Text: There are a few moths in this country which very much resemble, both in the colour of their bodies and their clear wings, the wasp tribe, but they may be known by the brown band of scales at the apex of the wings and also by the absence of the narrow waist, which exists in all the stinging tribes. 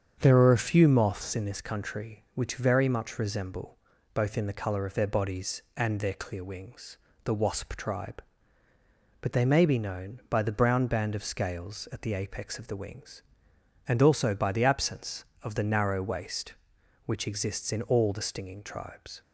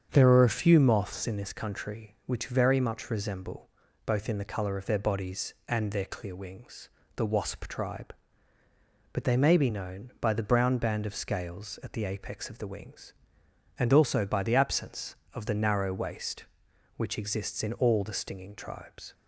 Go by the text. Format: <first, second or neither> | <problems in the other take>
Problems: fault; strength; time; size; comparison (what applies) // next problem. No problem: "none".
neither | starts louder than the rest; strong; the same in both